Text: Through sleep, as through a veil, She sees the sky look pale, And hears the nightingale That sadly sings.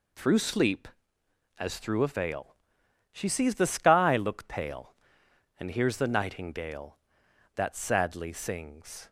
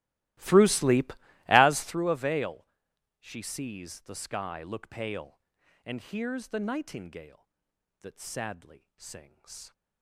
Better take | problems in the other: first | starts louder than the rest; strong; until 2.0 s; 17.5 dB

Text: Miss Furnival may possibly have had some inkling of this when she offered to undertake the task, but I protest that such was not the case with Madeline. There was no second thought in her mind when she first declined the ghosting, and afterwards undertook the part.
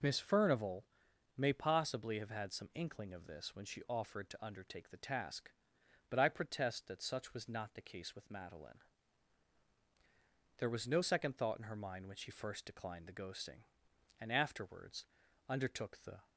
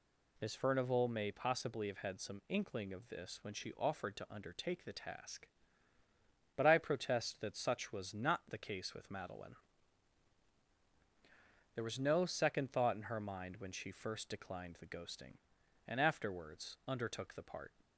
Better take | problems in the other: second | pauses between "Furnival" and "may"; noticeable; at 0.8 s; 0.54 s long // pauses between "afterwards" and "undertook"; at 15.0 s; 0.42 s long // stops before "part"; at 16.2 s

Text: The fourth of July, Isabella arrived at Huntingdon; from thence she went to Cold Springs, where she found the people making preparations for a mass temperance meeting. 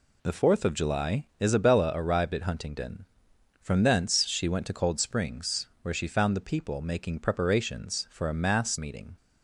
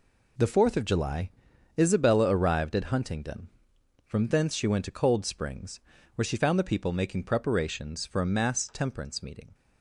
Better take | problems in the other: second | skips "temperance"; at 8.7 s

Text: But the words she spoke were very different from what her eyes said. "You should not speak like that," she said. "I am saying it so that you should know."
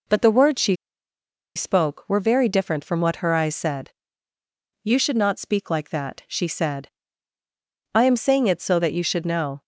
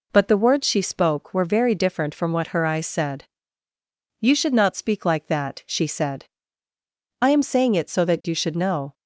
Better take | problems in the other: second | pauses between "she" and "spoke"; noticeable; at 0.7 s; 0.81 s long

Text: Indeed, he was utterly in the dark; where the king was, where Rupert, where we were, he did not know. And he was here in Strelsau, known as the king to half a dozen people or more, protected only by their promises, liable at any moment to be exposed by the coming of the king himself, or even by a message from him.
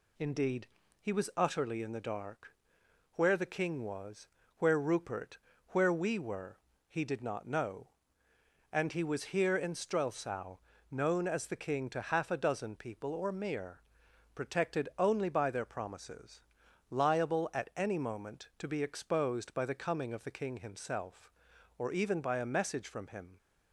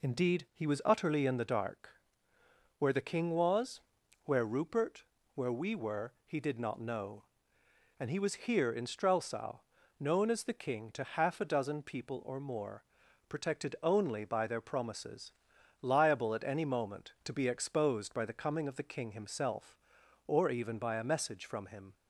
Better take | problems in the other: second | says "mere" for "more"; at 13.3 s

